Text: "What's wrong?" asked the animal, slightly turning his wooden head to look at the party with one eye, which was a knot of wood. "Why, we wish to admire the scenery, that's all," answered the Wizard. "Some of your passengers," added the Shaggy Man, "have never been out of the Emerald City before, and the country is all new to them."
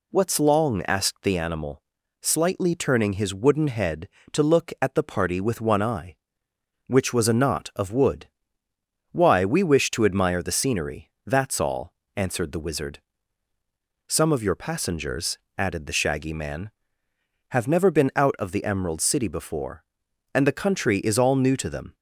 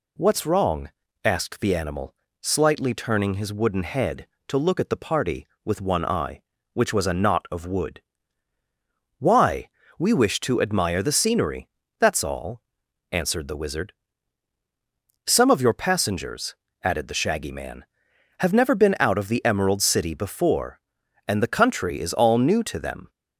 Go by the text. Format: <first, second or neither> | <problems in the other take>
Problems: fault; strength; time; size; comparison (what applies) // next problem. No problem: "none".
second | says "long" for "wrong"; at 0.4 s